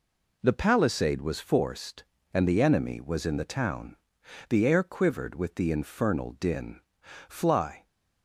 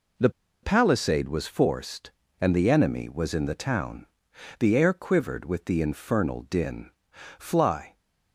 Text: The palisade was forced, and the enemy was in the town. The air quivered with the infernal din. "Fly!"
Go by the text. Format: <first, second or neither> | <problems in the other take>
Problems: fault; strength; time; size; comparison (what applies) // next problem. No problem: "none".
first | pauses between "The" and "palisade"; slight; at 0.3 s; 0.32 s long